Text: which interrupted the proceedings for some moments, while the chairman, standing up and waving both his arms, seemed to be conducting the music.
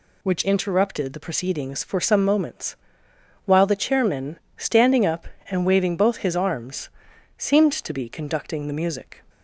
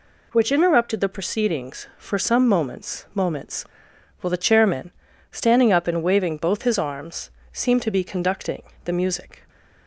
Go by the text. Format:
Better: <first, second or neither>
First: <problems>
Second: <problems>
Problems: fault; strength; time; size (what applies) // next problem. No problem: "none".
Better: first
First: none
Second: says "moments" twice; at 3.1 s // pauses between "conducting" and "the"; slight; at 8.6 s; 0.22 s long